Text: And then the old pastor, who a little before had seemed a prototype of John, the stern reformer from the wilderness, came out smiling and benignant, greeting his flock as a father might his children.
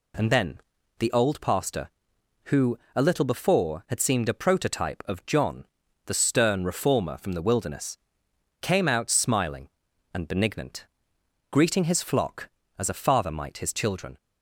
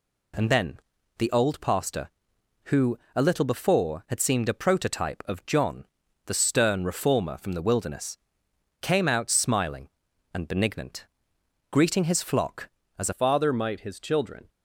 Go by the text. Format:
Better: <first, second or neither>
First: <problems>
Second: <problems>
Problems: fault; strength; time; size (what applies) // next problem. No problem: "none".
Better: first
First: pauses between "then" and "the"; at 0.5 s; 0.40 s long // pauses between "who" and "a"; slight; at 2.7 s; 0.16 s long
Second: pauses between "then" and "the"; at 0.7 s; 0.40 s long // pauses between "who" and "a"; slight; at 2.9 s; 0.16 s long // changes voice at "father"; from 13.1 s on; 1.3 s long